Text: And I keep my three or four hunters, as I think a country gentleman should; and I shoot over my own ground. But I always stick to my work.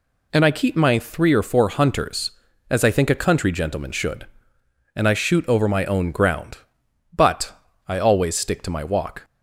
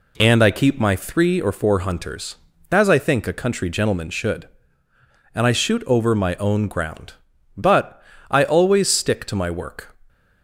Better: second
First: pauses between "But" and "I"; slight; at 7.5 s; 0.36 s long // says "walk" for "work"; at 8.8 s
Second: pauses between "But" and "I"; slight; at 8.0 s; 0.28 s long

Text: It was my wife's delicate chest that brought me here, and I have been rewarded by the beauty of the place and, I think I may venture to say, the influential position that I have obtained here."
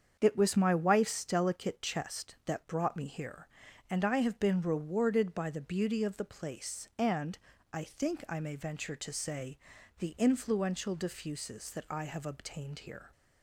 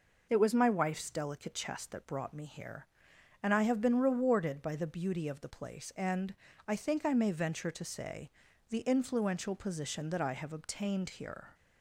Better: second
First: starts louder than the rest; strong; until 1.2 s; 7 dB // says "diffuses" for "position"; at 10.9 s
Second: none

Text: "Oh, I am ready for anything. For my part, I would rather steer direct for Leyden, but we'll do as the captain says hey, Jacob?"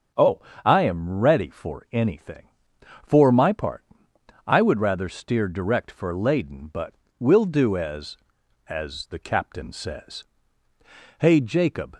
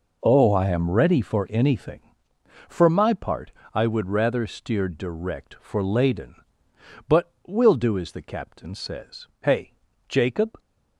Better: second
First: starts louder than the rest; until 1.3 s; 7 dB // pauses between "but" and "we'll"; slight; at 6.9 s; 0.26 s long // says "as" twice; at 8.6 s // pauses between "says" and "hey"; noticeable; at 10.2 s; 0.98 s long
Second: pauses between "but" and "we'll"; slight; at 7.3 s; 0.16 s long

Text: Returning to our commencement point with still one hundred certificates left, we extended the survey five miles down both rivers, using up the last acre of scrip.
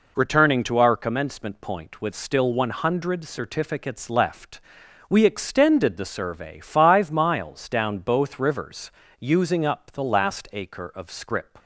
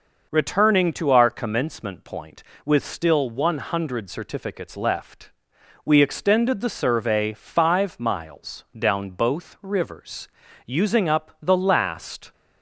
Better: first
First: none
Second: stops before "acre of scrip"; at 12.3 s

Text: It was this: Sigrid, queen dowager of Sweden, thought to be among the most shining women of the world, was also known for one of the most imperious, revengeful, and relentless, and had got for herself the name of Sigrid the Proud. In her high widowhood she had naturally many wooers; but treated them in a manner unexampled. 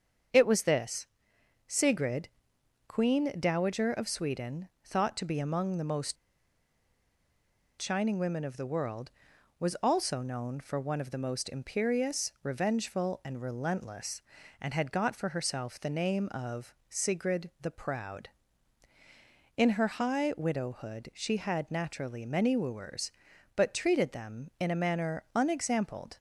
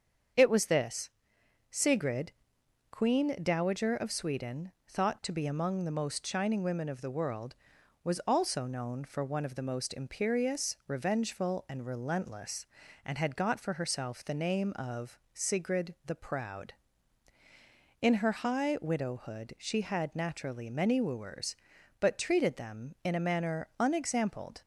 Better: second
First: starts louder than the rest; strong; until 1.9 s; 7 dB // pauses between "most" and "shining"; strong; at 6.1 s; 1.6 s long // pauses between "of" and "Sigrid"; slight; at 16.7 s; 0.16 s long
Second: starts louder than the rest; strong; until 1.9 s; 7 dB // pauses between "of" and "Sigrid"; slight; at 15.1 s; 0.16 s long

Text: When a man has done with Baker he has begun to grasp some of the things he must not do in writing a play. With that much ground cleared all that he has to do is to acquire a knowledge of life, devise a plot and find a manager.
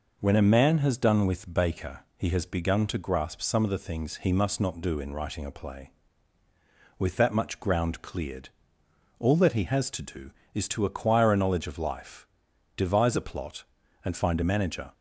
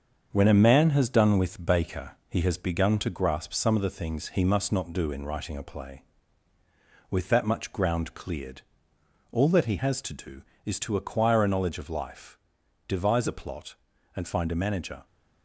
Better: first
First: pauses between "Baker" and "he"; slight; at 2.0 s; 0.16 s long // pauses between "cleared" and "all"; noticeable; at 8.4 s; 0.72 s long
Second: gets quieter; noticeable; throughout; 4.5 dB // pauses between "Baker" and "he"; slight; at 2.1 s; 0.16 s long // pauses between "cleared" and "all"; noticeable; at 8.6 s; 0.72 s long

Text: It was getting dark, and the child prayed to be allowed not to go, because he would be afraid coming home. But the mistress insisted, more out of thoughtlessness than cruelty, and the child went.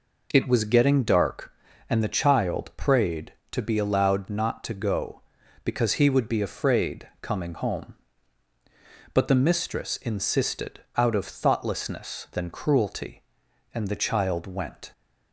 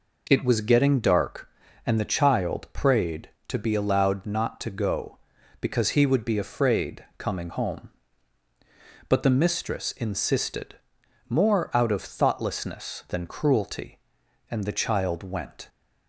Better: second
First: skips "more"; at 10.8 s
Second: none

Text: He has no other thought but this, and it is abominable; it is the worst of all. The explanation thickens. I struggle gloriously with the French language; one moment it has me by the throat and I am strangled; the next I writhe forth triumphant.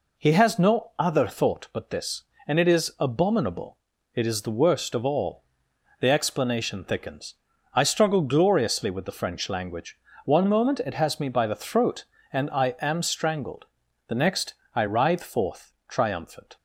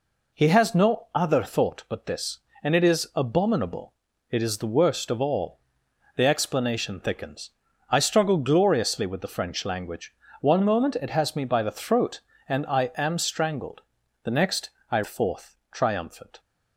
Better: first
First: pauses between "next" and "I"; slight; at 14.5 s; 0.20 s long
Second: pauses between "next" and "I"; slight; at 14.6 s; 0.20 s long // skips "writhe"; at 15.0 s

